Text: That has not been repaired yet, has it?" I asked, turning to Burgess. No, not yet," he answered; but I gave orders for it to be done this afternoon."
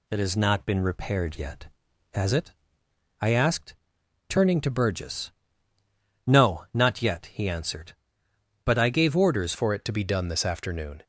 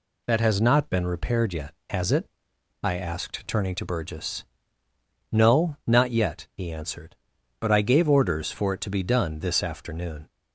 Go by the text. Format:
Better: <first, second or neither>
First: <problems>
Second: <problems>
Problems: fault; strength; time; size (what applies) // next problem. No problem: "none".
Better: second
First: changes voice at "for"; from 9.5 s on; 1.5 s long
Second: none